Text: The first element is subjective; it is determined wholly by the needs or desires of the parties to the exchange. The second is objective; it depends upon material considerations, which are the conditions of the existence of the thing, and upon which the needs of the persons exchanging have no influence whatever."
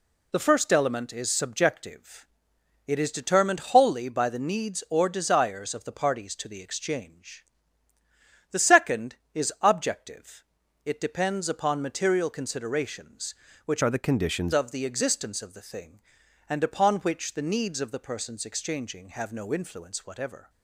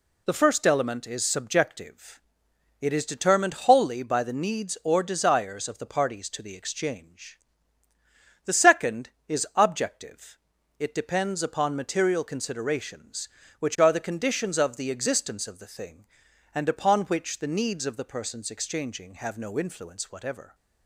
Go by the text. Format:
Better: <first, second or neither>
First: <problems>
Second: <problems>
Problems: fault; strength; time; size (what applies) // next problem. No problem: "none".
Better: second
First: changes voice from "are" to "conditions"; from 13.8 to 14.5 s; 0.7 s long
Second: none